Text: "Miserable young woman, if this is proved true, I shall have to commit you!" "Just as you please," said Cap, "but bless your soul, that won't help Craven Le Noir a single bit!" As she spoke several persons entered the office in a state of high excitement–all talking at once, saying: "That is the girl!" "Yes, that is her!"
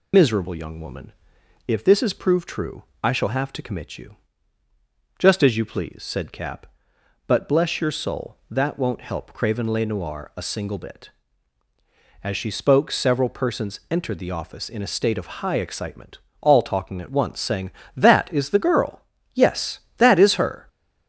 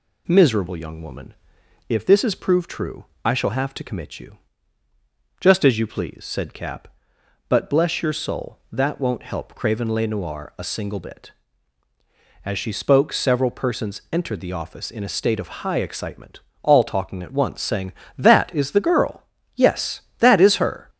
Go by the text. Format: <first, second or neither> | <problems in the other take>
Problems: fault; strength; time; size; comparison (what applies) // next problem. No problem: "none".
second | loses the start of "Miserable"; at 0.1 s; 80 ms